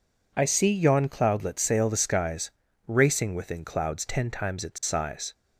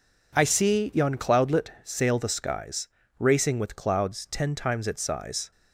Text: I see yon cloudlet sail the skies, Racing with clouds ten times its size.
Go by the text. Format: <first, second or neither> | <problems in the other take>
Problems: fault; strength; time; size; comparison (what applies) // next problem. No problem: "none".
second | says "within" for "with"; at 3.3 s